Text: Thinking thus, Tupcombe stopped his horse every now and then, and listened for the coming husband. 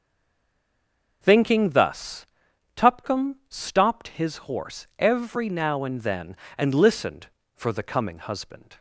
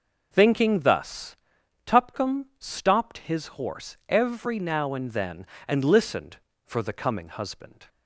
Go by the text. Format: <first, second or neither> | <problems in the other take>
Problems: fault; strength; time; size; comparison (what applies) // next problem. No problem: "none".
second | stays silent before the first word; noticeable; until 1.2 s; 1.2 s long